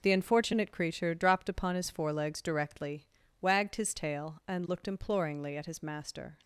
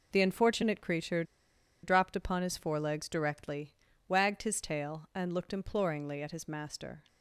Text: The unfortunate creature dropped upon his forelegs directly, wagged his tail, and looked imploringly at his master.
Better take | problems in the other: first | pauses between "creature" and "dropped"; noticeable; at 1.2 s; 0.60 s long

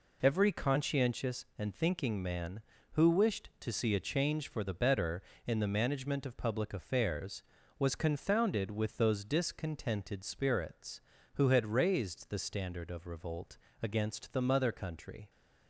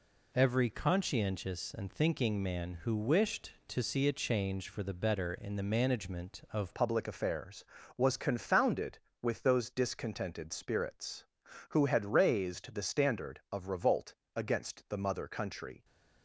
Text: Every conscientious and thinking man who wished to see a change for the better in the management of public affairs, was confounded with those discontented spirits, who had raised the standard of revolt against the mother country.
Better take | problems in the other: first | changes voice at "public"; from 6.7 s on; 9.1 s long // pauses between "revolt" and "against"; slight; at 14.1 s; 0.20 s long; slight in the first

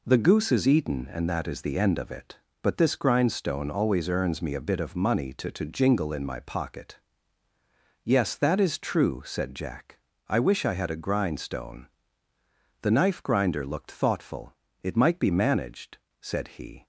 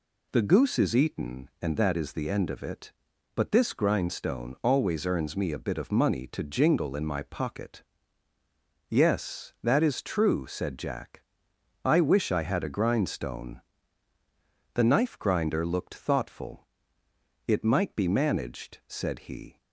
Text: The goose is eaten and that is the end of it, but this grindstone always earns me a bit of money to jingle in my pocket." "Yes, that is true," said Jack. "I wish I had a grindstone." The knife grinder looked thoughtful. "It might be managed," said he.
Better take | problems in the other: second | says "to" twice; at 5.5 s

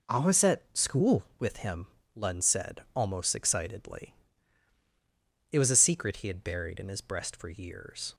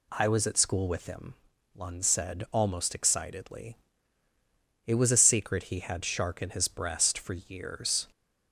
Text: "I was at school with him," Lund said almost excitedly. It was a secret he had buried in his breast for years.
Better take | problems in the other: first | says "shark" for "buried"; at 6.0 s

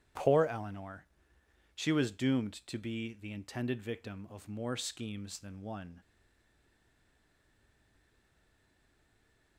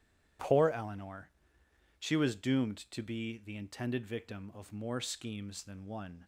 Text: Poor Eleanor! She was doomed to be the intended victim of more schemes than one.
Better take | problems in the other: second | starts louder than the rest; strong; until 1.8 s; 11 dB; strong in the second // stays silent after the last word; strong; from 6.0 s on; 3.5 s long

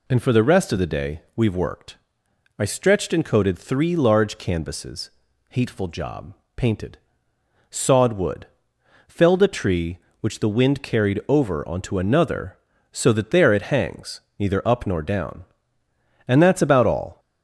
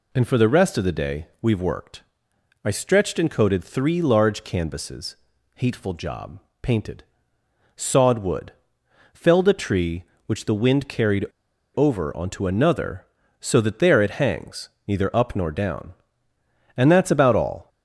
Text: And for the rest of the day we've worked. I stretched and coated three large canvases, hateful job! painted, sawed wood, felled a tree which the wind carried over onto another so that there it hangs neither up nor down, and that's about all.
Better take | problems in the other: first | pauses between "carried" and "over"; noticeable; at 11.2 s; 0.50 s long // pauses between "hangs" and "neither"; slight; at 14.6 s; 0.18 s long; slight in the first

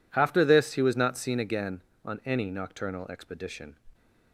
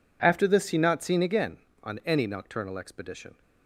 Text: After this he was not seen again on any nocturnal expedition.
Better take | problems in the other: first | skips "was"; at 0.7 s

